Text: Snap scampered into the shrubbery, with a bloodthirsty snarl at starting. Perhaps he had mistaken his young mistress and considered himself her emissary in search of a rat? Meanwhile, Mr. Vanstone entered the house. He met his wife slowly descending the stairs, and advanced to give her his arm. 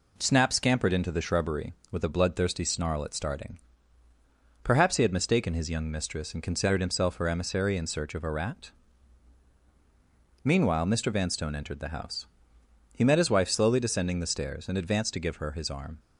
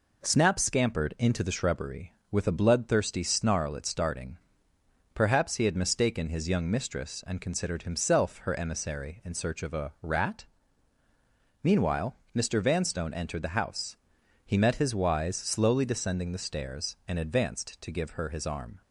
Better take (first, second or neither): first